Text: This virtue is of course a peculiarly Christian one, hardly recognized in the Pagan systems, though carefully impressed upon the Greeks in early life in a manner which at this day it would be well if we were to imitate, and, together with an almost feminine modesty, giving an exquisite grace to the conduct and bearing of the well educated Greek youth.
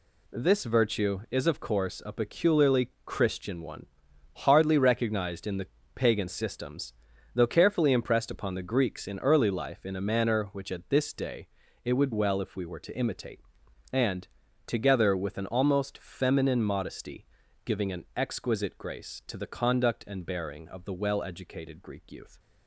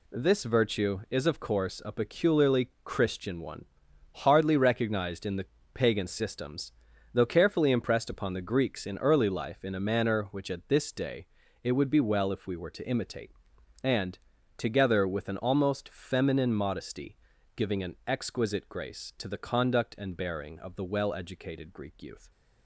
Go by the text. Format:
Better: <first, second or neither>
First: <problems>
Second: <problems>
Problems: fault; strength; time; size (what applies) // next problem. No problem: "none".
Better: second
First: pauses between "peculiarly" and "Christian"; slight; at 2.8 s; 0.16 s long // pauses between "the" and "Pagan"; slight; at 5.6 s; 0.28 s long // pauses between "day" and "it"; at 11.4 s; 0.38 s long // skips "be"; at 12.1 s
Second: pauses between "peculiarly" and "Christian"; slight; at 2.6 s; 0.15 s long // pauses between "the" and "Pagan"; slight; at 5.4 s; 0.28 s long // pauses between "day" and "it"; at 11.2 s; 0.38 s long